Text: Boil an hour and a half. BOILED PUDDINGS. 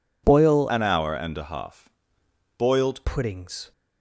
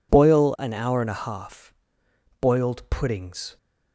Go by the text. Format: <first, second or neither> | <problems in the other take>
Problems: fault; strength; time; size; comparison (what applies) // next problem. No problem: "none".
second | changes voice from "an" to "BOILED"; from 0.6 to 3.0 s; 2.4 s long